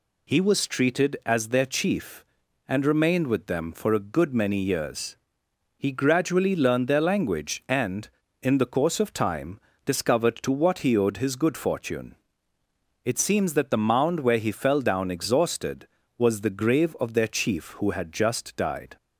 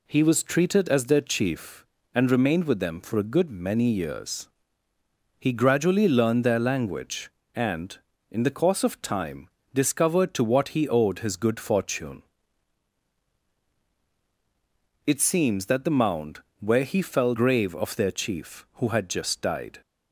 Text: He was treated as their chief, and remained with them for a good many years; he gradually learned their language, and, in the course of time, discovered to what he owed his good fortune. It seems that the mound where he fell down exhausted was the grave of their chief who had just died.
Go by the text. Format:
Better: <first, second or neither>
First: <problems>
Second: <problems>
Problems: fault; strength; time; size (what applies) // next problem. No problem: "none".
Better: first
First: none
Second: pauses between "mound" and "where"; slight; at 16.3 s; 0.22 s long // skips "down exhausted was the"; at 17.3 s